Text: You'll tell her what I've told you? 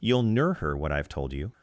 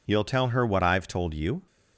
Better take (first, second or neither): second